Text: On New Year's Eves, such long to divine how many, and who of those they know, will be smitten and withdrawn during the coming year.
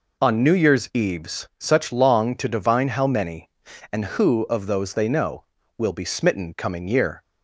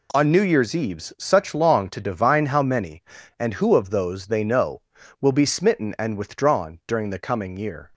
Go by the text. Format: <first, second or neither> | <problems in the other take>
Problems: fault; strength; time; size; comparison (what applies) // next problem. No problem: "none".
second | skips "and withdrawn during the"; at 6.5 s